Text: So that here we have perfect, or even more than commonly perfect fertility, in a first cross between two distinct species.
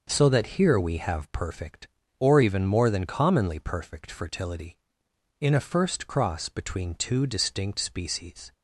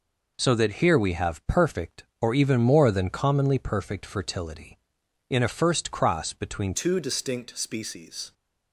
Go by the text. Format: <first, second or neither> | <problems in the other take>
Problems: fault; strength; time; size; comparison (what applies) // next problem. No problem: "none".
first | changes voice at "two"; from 6.7 s on; 1.6 s long